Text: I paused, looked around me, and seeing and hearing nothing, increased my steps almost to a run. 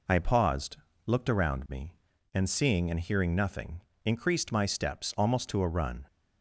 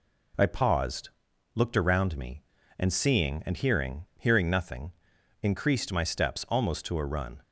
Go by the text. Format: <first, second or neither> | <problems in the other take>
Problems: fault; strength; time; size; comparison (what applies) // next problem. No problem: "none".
first | says "hearing" twice; at 4.1 s